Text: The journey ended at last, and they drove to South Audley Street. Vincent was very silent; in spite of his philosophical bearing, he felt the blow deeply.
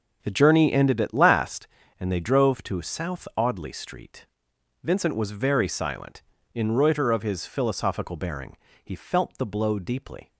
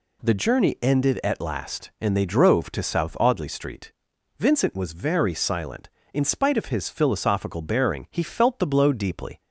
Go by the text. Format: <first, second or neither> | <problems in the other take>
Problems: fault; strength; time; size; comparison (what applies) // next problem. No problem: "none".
second | says "reuter" for "spite"; at 6.7 s